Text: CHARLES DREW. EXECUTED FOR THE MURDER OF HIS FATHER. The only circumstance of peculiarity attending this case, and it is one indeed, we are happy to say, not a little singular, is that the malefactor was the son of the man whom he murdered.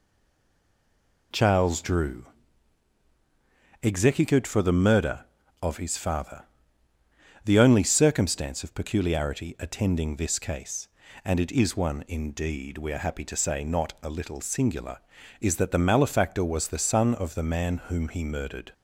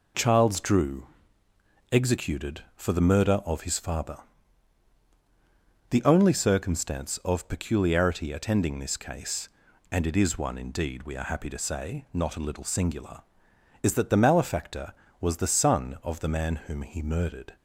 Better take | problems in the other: second | stays silent before the first word; noticeable; until 1.3 s; 1.3 s long

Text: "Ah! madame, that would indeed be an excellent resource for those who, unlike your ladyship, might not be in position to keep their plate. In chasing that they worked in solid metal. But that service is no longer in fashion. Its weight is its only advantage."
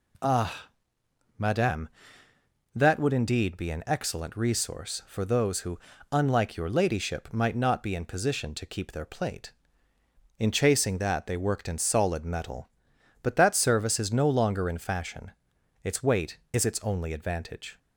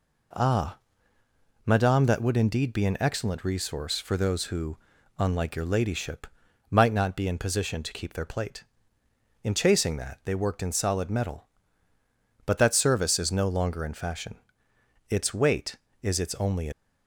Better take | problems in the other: first | stops before "advantage"; at 16.7 s

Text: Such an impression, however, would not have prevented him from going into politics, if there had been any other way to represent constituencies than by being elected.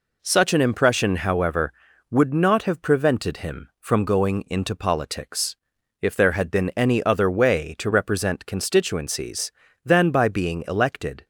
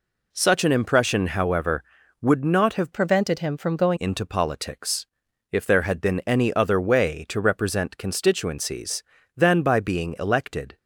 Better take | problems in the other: first | changes voice from "prevented" to "going"; from 2.9 to 3.9 s; 1.0 s long

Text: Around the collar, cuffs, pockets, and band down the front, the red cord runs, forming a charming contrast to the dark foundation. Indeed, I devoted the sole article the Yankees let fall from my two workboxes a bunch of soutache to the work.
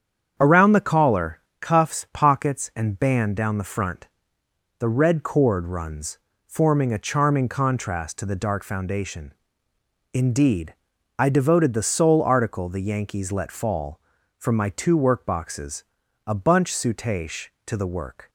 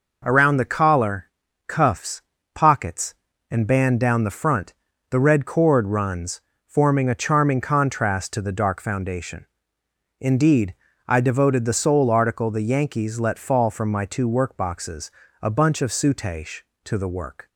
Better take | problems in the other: second | starts louder than the rest; strong; until 1.3 s; 8 dB // pauses between "workboxes" and "a"; at 15.8 s; 0.44 s long; slight in the second // skips "of"; at 16.7 s

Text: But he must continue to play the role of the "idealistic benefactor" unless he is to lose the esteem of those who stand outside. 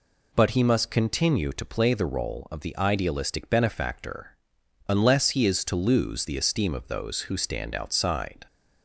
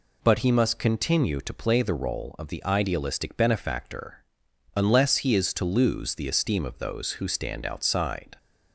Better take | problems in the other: neither | pauses between "benefactor" and "unless"; noticeable; the same in both

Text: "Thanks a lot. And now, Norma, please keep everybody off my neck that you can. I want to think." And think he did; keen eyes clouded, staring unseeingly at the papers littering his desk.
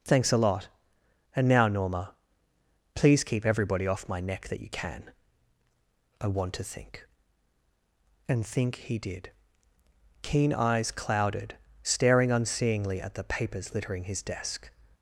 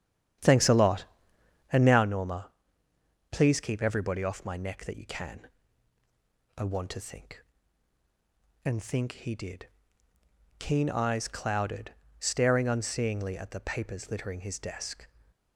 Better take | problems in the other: first | starts louder than the rest; strong; until 2.1 s; 9.5 dB

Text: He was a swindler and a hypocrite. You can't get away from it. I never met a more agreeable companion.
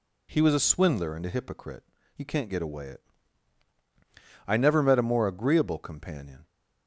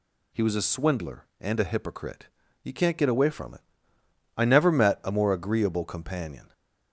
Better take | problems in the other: second | skips "from"; at 2.8 s

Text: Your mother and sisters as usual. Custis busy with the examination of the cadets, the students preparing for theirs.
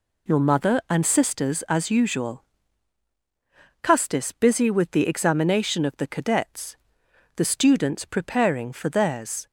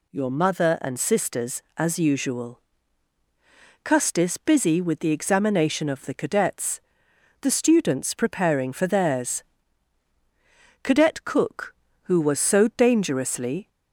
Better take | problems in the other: first | goes on to say "Cadet Cook who was so dangerously"; strong; from 10.8 s on; 2.8 s long

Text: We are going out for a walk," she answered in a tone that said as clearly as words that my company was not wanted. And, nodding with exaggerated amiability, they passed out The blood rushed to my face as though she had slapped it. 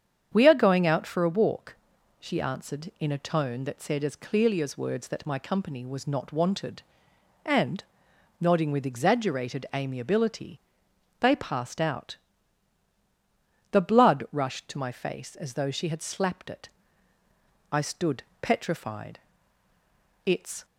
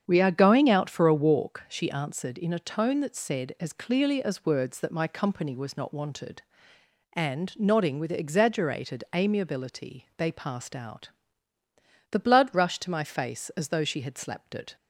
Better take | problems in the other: second | starts louder than the rest; strong; until 1.3 s; 8 dB; strong in the second // pauses between "out" and "The"; strong; at 12.1 s; 1.5 s long; also in the second // goes on to say "I stood petrified It's"; strong; from 17.7 s on; 2.9 s long

